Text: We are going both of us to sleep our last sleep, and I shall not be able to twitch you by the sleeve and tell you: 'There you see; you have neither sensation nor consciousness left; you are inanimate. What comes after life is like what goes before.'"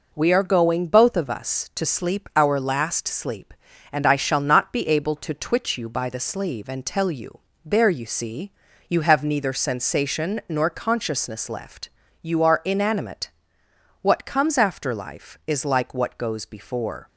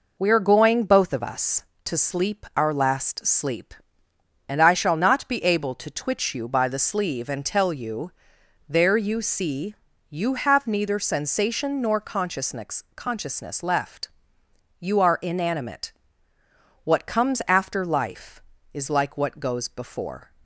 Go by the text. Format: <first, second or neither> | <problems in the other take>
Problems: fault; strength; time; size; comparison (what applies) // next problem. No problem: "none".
first | says "consciousness" twice; at 12.9 s